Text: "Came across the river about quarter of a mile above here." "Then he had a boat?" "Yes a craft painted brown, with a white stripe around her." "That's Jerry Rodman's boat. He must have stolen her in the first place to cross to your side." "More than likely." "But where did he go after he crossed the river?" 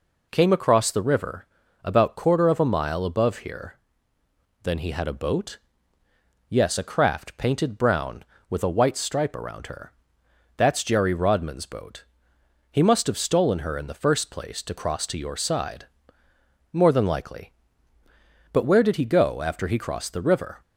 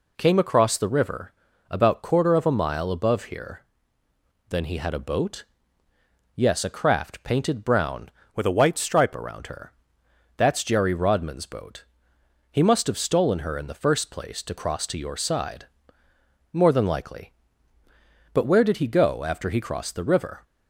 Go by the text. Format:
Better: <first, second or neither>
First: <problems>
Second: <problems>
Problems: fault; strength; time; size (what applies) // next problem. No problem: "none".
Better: first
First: pauses between "river" and "about"; slight; at 1.4 s; 0.36 s long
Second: pauses between "river" and "about"; slight; at 1.3 s; 0.36 s long // changes voice from "with" to "stripe"; from 8.3 to 9.1 s; 0.8 s long